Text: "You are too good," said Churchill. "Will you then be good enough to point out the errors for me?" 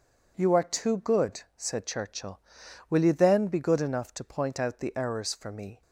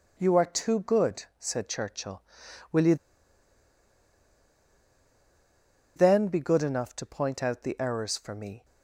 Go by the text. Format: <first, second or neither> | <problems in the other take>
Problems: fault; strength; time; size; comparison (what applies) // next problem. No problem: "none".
first | pauses between "you" and "then"; strong; at 2.9 s; 3.0 s long